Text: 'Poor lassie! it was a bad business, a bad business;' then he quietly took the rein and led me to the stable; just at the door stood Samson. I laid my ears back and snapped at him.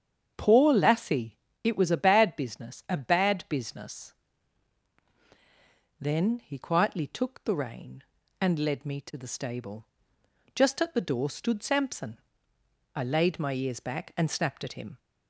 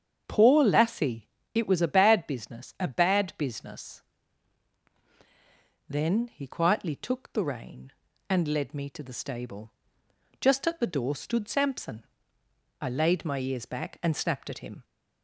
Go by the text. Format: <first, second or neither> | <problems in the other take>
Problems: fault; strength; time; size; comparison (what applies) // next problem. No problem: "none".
neither | starts louder than the rest; strong; the same in both